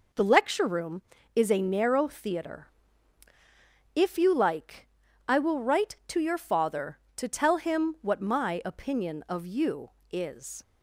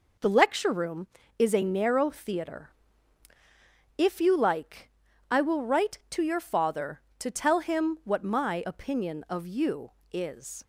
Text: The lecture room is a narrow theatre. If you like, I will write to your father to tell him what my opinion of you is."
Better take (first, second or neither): neither